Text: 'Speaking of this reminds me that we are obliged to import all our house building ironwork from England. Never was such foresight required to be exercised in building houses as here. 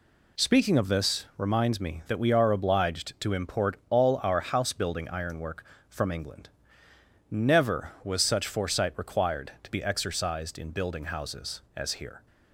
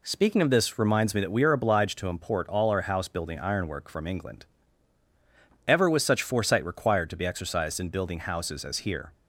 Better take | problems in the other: first | says "Ever" for "Never"; at 5.6 s

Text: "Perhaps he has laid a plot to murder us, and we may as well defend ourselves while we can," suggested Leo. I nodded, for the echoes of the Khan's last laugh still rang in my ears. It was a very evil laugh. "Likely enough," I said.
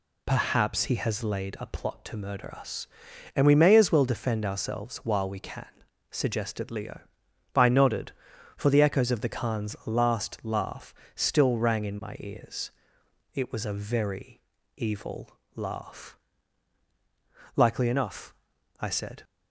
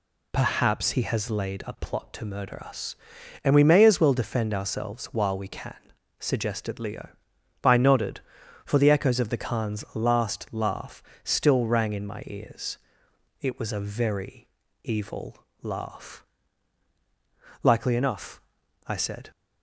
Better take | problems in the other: neither | pauses between "laugh" and "still"; slight; the same in both // pauses between "very" and "evil"; the same in both // pauses between "evil" and "laugh"; slight; the same in both

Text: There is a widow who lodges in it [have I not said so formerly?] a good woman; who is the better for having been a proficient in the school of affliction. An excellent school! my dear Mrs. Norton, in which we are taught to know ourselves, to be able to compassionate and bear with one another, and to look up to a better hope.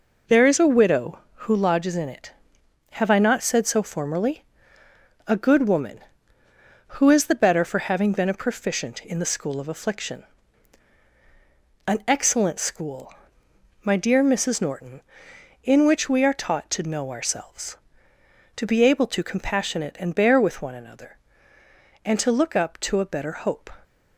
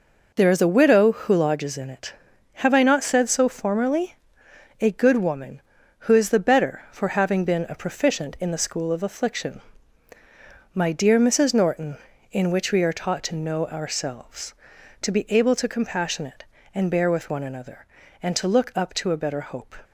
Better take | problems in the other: first | skips "An excellent school"; at 10.1 s

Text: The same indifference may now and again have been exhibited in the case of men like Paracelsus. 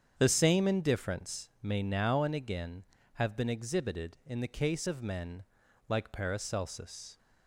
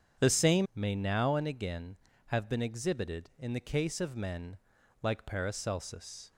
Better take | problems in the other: first | starts louder than the rest; strong; until 1.2 s; 7.5 dB; strong in the first // skips "indifference"; at 0.7 s // pauses between "men" and "like"; noticeable; at 4.5 s; 0.46 s long; noticeable in the first

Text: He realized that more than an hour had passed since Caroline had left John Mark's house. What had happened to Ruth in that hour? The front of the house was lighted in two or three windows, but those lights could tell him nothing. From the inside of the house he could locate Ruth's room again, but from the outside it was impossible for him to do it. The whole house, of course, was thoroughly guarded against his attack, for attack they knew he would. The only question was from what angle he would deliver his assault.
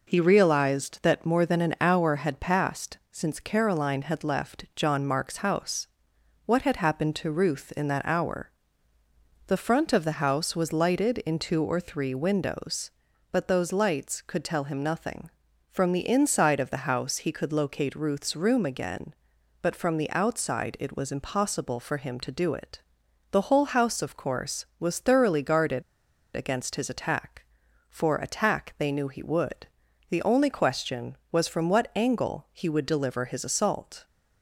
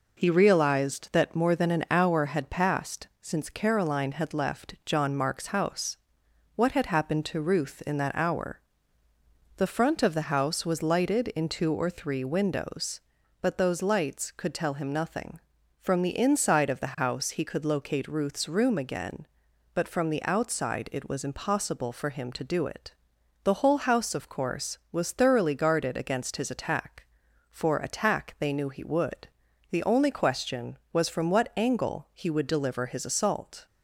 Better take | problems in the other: second | pauses between "passed" and "since"; slight; at 2.9 s; 0.16 s long; slight in the second // pauses between "guarded" and "against"; noticeable; at 25.8 s; 0.52 s long

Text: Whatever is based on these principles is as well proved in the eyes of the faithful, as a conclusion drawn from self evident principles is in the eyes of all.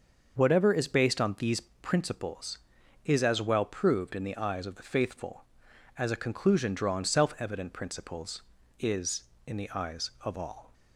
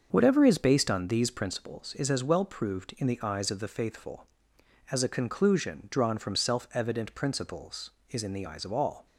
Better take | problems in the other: second | starts louder than the rest; until 1.4 s; 6 dB; also in the second // skips "from"; at 7.0 s

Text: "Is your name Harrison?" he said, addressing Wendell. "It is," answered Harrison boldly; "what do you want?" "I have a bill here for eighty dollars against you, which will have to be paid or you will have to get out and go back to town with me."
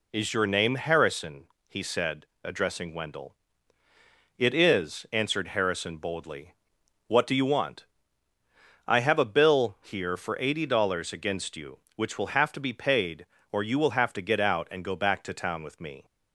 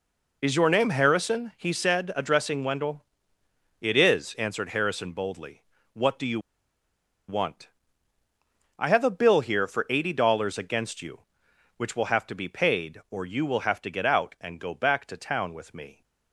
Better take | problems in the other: first | pauses between "you" and "want"; noticeable; at 6.3 s; 0.88 s long

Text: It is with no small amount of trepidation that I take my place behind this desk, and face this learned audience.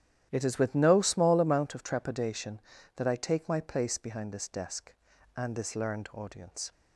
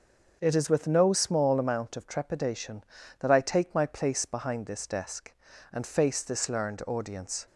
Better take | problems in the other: second | starts louder than the rest; strong; until 1.3 s; 11 dB; also in the second // skips "face"; at 5.5 s

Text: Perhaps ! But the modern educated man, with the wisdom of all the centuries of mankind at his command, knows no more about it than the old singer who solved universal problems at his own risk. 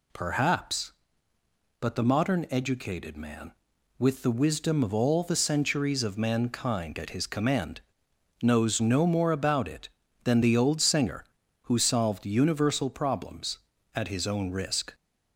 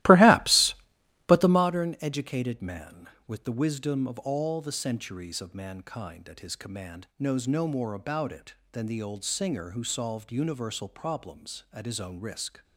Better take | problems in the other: first | starts louder than the rest; strong; until 1.7 s; 16.5 dB

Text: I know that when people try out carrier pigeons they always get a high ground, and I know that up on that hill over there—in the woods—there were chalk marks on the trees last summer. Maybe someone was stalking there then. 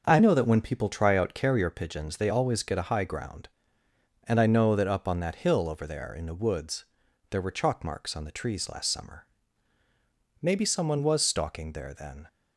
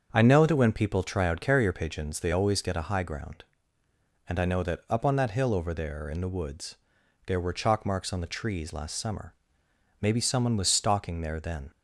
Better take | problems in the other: neither | starts louder than the rest; the same in both

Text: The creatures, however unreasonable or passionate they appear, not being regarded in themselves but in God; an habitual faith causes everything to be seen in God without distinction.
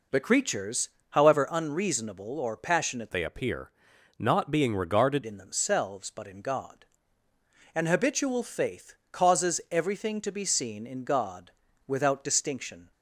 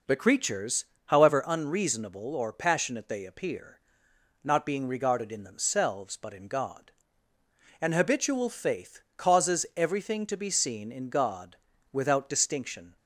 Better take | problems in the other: second | changes voice from "they" to "regarded"; from 3.1 to 5.2 s; 2.1 s long // pauses between "faith" and "causes"; slight; at 8.9 s; 0.18 s long; slight in the second // pauses between "God" and "without"; at 11.4 s; 0.38 s long; also in the second

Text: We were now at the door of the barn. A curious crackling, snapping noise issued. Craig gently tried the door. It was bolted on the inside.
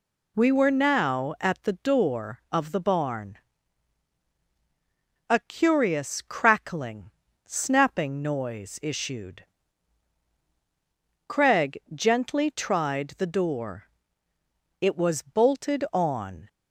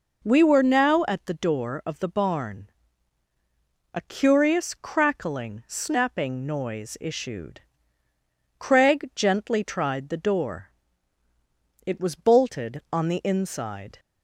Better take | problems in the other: second | pauses between "Craig" and "gently"; slight; at 11.7 s; 0.16 s long // stops before "the inside"; at 16.4 s

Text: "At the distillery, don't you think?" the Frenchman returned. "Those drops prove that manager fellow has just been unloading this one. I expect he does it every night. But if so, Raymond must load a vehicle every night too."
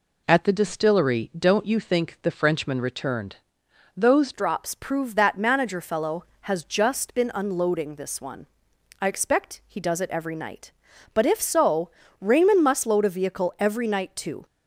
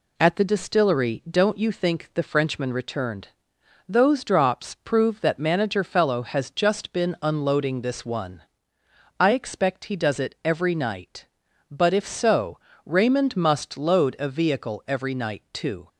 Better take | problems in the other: second | changes voice at "drops"; from 4.3 s on; 10.1 s long

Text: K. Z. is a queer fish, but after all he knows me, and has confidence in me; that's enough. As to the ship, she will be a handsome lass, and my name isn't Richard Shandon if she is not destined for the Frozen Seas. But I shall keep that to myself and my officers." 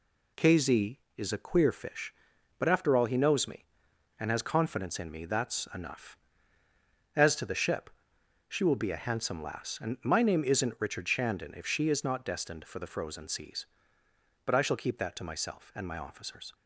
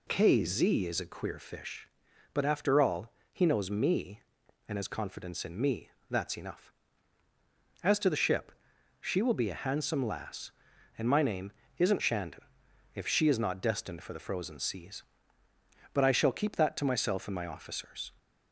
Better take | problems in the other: first | pauses between "all" and "he"; slight; at 3.1 s; 0.20 s long // pauses between "name" and "isn't"; slight; at 11.5 s; 0.24 s long // skips "Richard"; at 12.0 s // pauses between "Shandon" and "if"; noticeable; at 12.4 s; 0.50 s long

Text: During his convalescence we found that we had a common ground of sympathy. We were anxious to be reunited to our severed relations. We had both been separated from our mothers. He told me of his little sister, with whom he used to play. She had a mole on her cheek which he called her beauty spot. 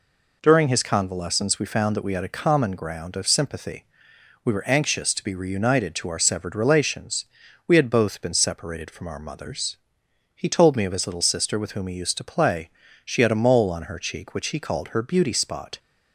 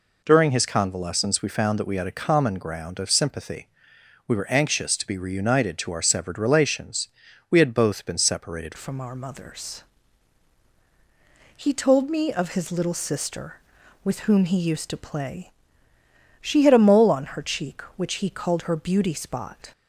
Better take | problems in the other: first | changes voice at "from"; from 8.7 s on; 11.0 s long

